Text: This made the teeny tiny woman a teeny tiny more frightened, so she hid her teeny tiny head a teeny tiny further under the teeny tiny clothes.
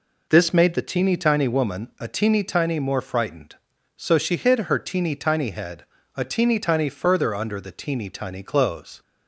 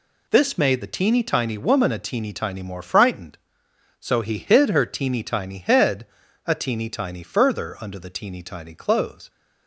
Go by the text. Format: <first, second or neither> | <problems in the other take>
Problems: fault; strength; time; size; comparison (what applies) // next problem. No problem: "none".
first | says "he" for "she"; at 4.2 s // pauses between "head" and "a"; at 6.0 s; 0.40 s long; slight in the first